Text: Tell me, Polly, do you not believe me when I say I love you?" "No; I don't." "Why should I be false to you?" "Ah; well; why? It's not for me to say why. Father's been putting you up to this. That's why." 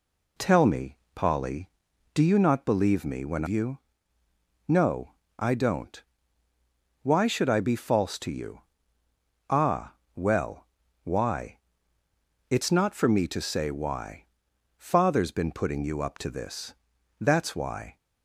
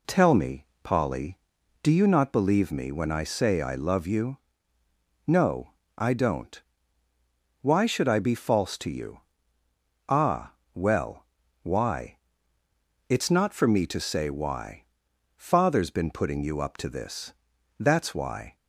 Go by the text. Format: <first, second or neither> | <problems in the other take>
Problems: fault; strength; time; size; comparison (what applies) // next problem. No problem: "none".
second | skips "I say I love"; at 3.4 s